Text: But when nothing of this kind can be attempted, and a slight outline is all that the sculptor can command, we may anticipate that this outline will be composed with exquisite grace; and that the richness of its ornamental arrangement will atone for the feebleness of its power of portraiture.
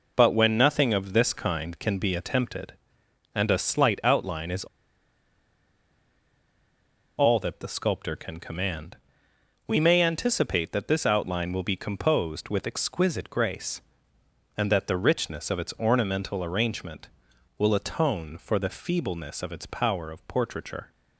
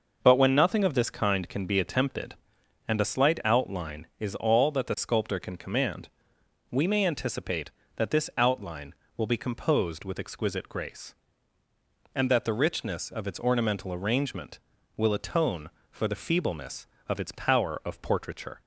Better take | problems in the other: second | pauses between "is" and "all"; strong; at 4.6 s; 2.5 s long

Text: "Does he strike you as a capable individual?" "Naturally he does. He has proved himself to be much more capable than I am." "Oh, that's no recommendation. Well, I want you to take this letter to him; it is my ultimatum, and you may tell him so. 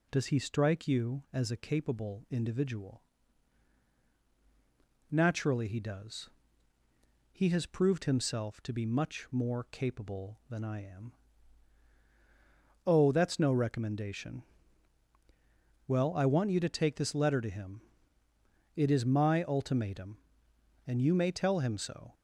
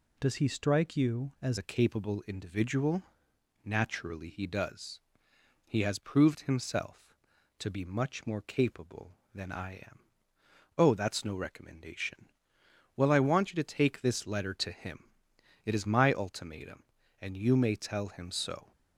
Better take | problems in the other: first | changes voice at "a"; from 1.5 s on; 17.2 s long

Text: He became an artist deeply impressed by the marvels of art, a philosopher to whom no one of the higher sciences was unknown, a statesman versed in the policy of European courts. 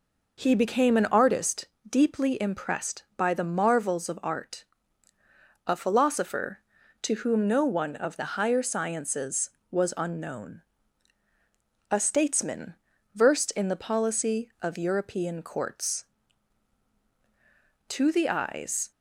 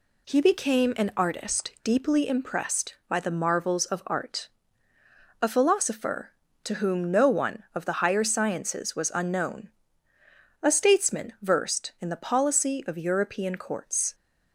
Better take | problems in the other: second | pauses between "artist" and "deeply"; slight; at 1.6 s; 0.22 s long // pauses between "statesman" and "versed"; at 12.7 s; 0.42 s long // goes on to say "To the eyes"; noticeable; from 17.8 s on; 1.0 s long

